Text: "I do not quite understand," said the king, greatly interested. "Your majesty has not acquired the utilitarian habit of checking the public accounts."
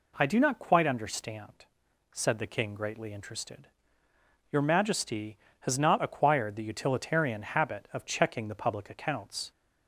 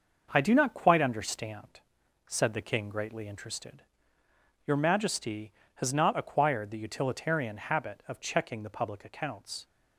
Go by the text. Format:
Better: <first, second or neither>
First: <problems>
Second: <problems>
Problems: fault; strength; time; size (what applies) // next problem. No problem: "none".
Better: first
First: none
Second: gets quieter; throughout; 6 dB